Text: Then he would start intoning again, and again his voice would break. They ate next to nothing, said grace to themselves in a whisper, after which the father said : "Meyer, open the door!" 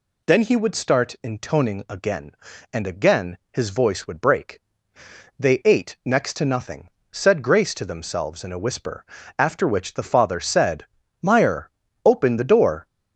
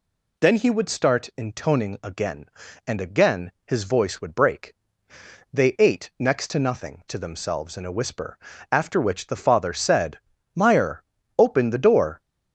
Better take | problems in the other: first | skips "said grace"; at 7.0 s

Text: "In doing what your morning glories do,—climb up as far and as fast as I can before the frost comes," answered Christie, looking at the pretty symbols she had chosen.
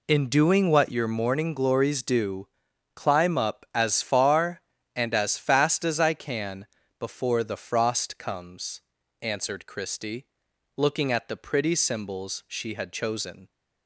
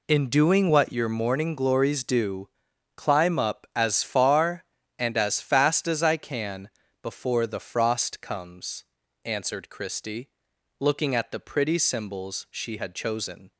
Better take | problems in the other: neither | pauses between "can" and "before"; slight; the same in both

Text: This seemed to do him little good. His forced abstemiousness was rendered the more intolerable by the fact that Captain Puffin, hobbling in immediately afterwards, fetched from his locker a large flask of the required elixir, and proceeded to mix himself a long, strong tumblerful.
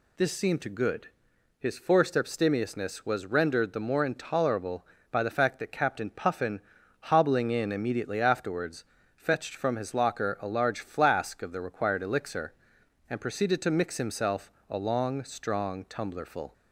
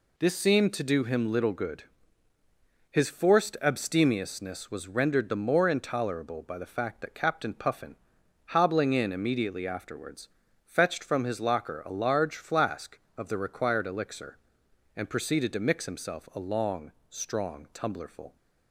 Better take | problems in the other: second | skips "do him little"; at 0.6 s // pauses between "himself" and "a"; slight; at 14.5 s; 0.18 s long

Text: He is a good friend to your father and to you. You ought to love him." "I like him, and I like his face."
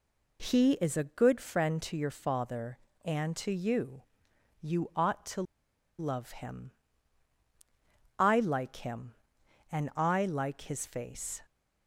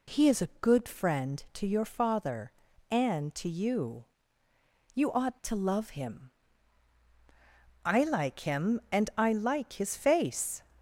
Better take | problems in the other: second | pauses between "to" and "love"; noticeable; at 5.4 s; 0.55 s long

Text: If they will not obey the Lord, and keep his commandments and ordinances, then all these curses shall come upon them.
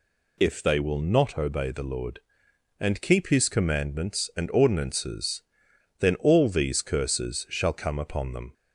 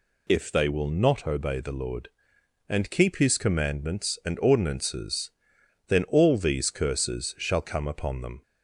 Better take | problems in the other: neither | none

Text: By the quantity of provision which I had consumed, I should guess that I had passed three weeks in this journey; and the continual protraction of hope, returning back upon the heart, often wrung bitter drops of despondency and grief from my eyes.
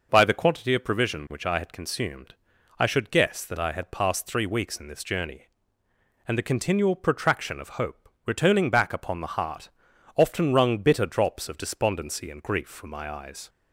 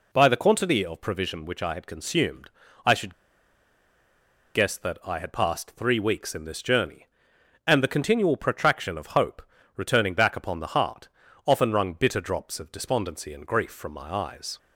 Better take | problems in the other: first | pauses between "should" and "guess"; strong; at 3.1 s; 1.4 s long

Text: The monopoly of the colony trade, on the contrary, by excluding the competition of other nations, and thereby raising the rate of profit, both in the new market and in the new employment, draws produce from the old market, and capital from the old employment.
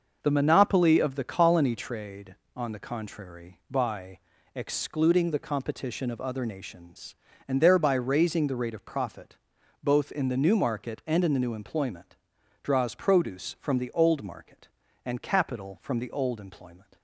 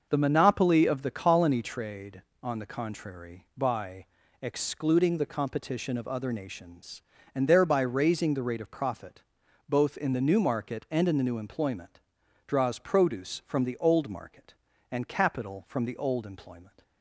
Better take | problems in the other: neither | starts louder than the rest; noticeable; the same in both // pauses between "by" and "excluding"; slight; the same in both

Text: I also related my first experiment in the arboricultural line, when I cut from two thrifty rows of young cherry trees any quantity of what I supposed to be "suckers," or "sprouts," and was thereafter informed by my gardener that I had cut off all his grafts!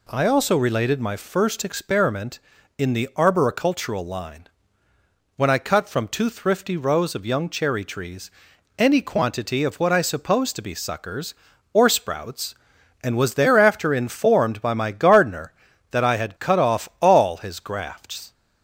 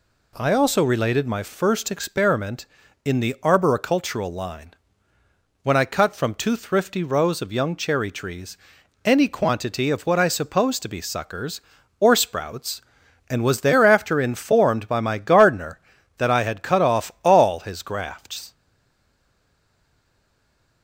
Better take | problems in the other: first | pauses between "trees" and "any"; noticeable; at 8.5 s; 0.48 s long; noticeable in the first // stays silent after the last word; from 18.5 s on; 2.3 s long

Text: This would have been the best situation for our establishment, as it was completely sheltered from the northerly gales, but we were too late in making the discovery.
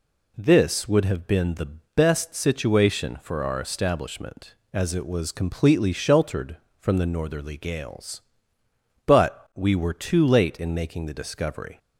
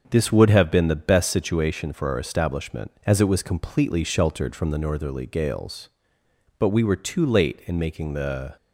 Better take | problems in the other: first | starts louder than the rest; until 1.1 s; 6.5 dB // stops before "discovery"; at 8.5 s

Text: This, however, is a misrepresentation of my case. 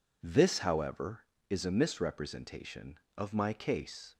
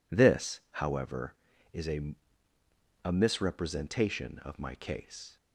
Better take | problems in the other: first | says "a" twice; at 3.0 s

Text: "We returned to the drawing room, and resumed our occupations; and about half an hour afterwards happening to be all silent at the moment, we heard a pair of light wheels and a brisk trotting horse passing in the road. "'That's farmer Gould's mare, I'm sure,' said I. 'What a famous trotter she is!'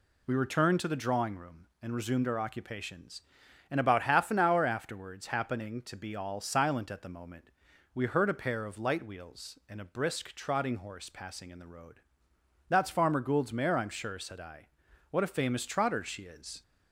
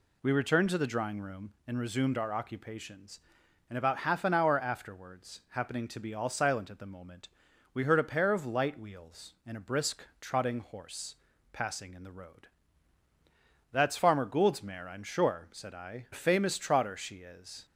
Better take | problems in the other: first | pauses between "brisk" and "trotting"; slight; at 10.0 s; 0.16 s long // pauses between "horse" and "passing"; at 11.1 s; 0.38 s long // skips "What"; at 16.0 s

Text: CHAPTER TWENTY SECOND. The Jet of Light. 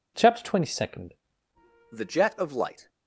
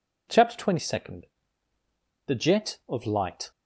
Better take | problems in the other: second | changes voice at "The"; from 1.9 s on; 0.9 s long

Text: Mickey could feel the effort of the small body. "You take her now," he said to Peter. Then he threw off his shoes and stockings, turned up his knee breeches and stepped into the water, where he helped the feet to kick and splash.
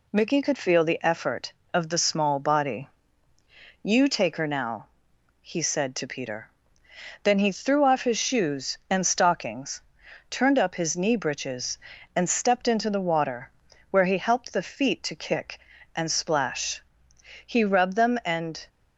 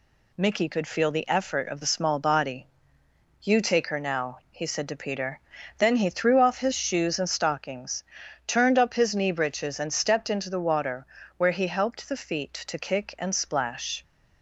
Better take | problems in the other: second | goes on to say "He rubbed them and"; noticeable; from 17.4 s on; 1.2 s long

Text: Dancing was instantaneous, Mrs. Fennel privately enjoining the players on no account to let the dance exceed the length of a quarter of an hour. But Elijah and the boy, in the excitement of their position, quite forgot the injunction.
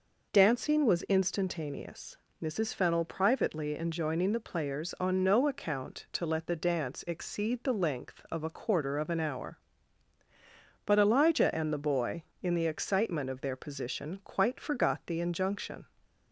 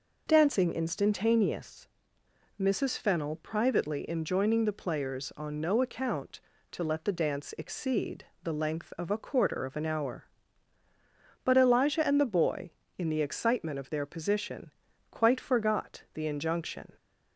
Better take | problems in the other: first | skips "was"; at 0.7 s // pauses between "exceed" and "the"; slight; at 8.2 s; 0.18 s long

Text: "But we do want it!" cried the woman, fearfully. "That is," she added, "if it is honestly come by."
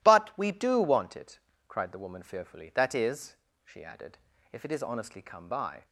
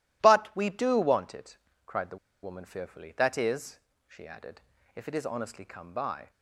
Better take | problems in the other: first | pauses between "the" and "woman"; slight; at 2.1 s; 0.27 s long

